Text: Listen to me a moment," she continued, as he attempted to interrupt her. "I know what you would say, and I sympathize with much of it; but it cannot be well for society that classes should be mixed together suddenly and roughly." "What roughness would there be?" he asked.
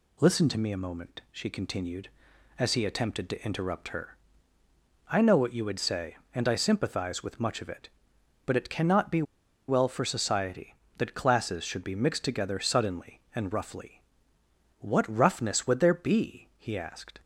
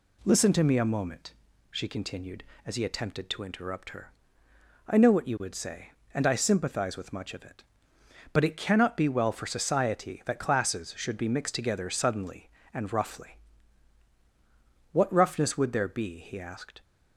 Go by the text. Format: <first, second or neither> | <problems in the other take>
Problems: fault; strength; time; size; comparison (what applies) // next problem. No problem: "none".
second | pauses between "be" and "well"; at 9.2 s; 0.44 s long